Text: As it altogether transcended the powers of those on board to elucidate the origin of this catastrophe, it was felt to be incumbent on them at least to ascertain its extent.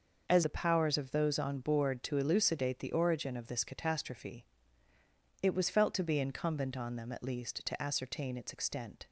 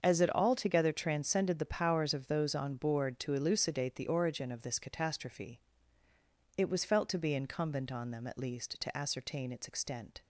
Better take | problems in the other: second | starts louder than the rest; noticeable; until 1.2 s; 6 dB; also in the second // skips "it altogether transcended"; at 0.4 s

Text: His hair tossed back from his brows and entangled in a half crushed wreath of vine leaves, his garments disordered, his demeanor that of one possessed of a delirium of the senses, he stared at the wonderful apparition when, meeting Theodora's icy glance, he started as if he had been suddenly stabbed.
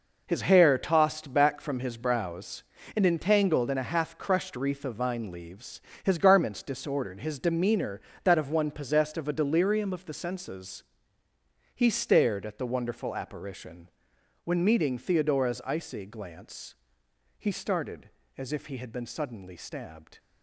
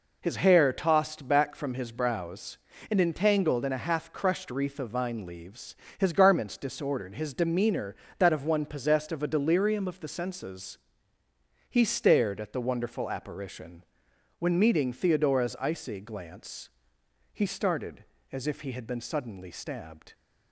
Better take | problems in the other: second | gets quieter; strong; throughout; 9.5 dB // pauses between "apparition" and "when"; noticeable; at 13.8 s; 0.56 s long; noticeable in the second

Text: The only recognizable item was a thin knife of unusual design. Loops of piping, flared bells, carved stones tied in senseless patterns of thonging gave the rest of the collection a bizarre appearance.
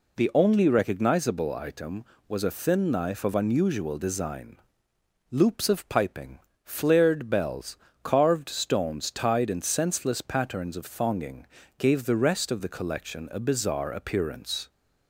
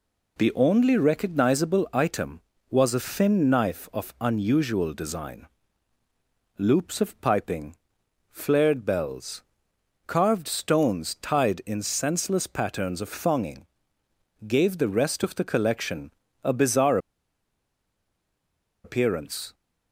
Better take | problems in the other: first | pauses between "thonging" and "gave"; noticeable; at 13.6 s; 0.82 s long; slight in the first // pauses between "collection" and "a"; slight; at 16.1 s; 0.32 s long // pauses between "bizarre" and "appearance"; strong; at 16.9 s; 1.8 s long

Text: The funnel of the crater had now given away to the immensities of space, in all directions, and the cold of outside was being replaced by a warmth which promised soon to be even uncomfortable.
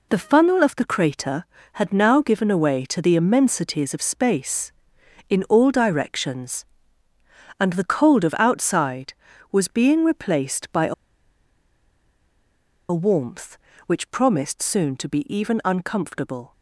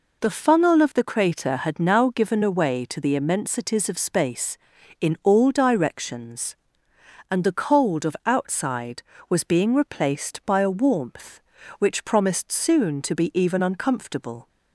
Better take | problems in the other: second | pauses between "a" and "warmth"; strong; at 10.9 s; 1.9 s long

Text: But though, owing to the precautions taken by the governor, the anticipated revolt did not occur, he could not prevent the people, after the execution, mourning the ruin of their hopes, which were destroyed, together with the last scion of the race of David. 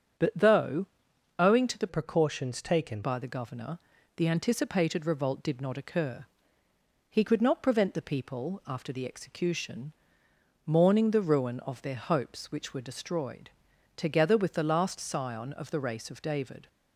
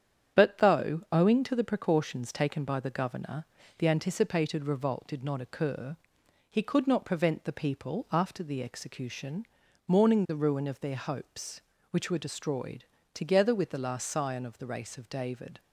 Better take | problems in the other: second | starts louder than the rest; strong; until 1.7 s; 8 dB; strong in the second // changes voice from "precautions" to "taken"; from 1.8 to 3.0 s; 1.2 s long

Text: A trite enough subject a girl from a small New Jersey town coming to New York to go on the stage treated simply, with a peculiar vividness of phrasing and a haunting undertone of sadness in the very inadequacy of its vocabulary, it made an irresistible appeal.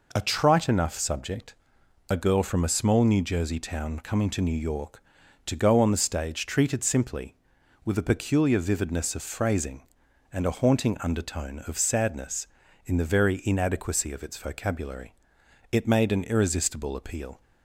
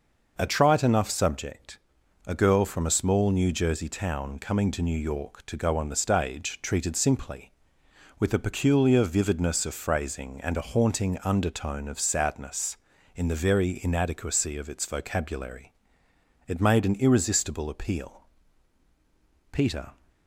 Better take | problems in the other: first | pauses between "subject" and "a"; noticeable; at 1.7 s; 0.48 s long; noticeable in the first // goes on to say "Peter"; slight; from 19.5 s on; 0.44 s long

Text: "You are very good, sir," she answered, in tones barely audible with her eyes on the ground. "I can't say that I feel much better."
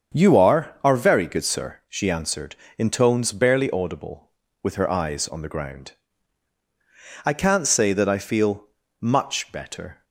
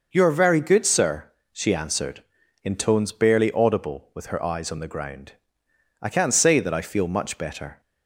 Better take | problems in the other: second | starts louder than the rest; strong; until 1.2 s; 7 dB // says "are" twice; at 0.8 s // pauses between "feel" and "much"; slight; at 8.6 s; 0.32 s long

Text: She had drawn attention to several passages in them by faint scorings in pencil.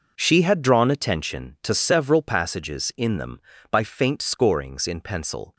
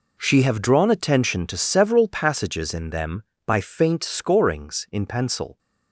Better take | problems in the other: first | says "have" for "had"; at 0.4 s

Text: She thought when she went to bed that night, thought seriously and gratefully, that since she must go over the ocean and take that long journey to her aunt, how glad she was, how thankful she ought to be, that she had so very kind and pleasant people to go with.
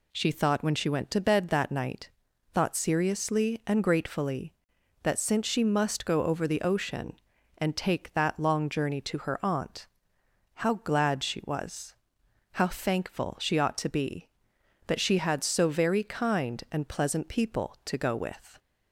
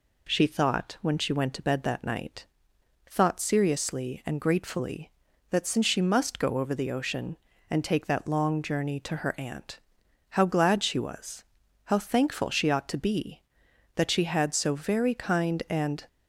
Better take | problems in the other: first | stops before "pleasant people to go with"; at 16.0 s

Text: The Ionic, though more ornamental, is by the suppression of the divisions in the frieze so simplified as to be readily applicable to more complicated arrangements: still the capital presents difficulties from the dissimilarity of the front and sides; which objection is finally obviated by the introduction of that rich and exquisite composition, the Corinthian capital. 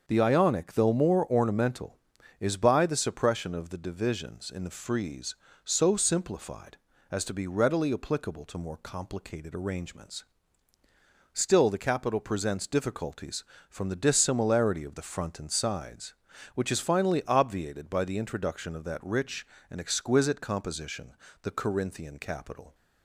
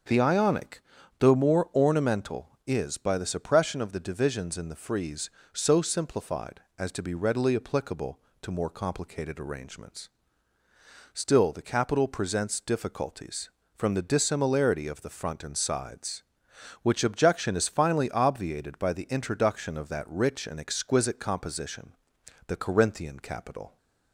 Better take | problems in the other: second | starts louder than the rest; until 1.0 s; 6.5 dB; also in the second // skips "objection"; at 16.7 s

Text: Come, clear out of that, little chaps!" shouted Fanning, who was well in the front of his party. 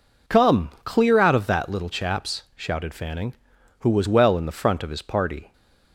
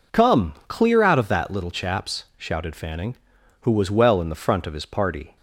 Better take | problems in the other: neither | none

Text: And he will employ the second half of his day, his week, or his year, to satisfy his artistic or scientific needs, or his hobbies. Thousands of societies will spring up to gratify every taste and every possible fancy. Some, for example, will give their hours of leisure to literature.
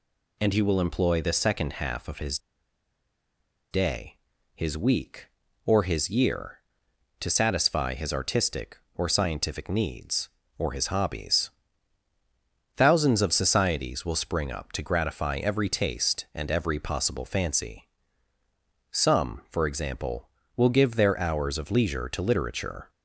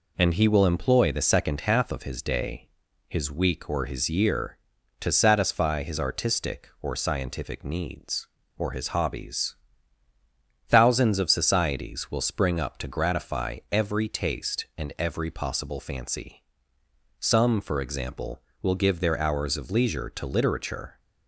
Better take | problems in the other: second | pauses between "his" and "day"; strong; at 2.3 s; 1.3 s long

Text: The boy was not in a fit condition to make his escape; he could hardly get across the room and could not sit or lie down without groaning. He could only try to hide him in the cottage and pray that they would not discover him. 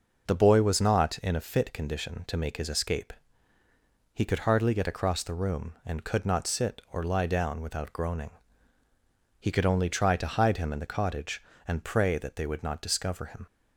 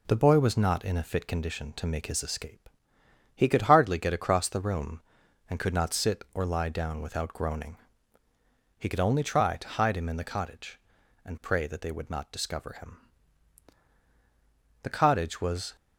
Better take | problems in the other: first | goes on to say "The cottage was"; noticeable; from 14.8 s on; 0.94 s long

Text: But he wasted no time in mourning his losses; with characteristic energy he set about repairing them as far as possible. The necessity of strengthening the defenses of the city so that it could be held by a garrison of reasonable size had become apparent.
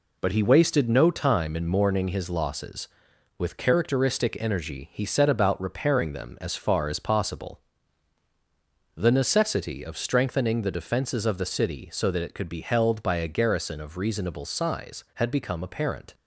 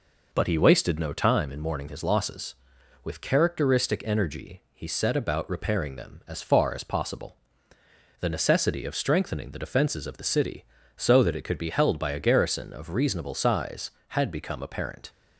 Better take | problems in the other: neither | none

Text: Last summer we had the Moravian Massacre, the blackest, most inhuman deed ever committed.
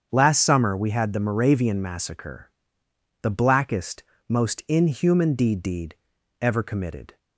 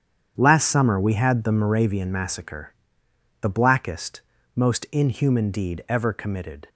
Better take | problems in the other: second | starts louder than the rest; strong; until 1.1 s; 7.5 dB; strong in the second // says "deed" twice; at 5.6 s

